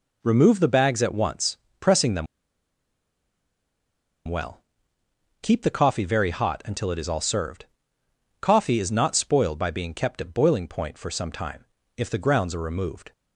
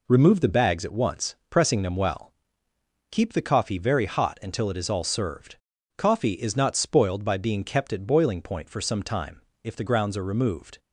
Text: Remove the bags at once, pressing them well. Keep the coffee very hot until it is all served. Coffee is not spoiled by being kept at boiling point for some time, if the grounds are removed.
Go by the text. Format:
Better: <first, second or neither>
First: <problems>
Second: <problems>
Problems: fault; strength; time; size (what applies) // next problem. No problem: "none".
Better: second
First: pauses between "them" and "well"; strong; at 2.2 s; 2.0 s long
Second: none